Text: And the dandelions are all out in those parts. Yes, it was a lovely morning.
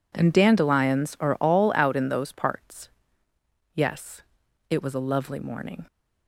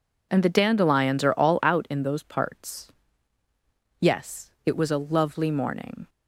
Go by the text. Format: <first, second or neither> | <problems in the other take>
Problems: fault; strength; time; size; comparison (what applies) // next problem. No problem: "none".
second | skips "the"; at 0.3 s